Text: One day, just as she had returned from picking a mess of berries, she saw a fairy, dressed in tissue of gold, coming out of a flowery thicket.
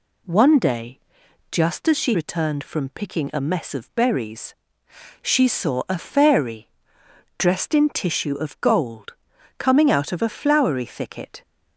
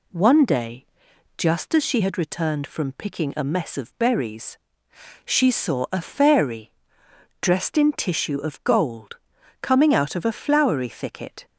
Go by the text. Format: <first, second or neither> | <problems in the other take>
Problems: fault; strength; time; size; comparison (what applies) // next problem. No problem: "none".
second | skips "had"; at 2.1 s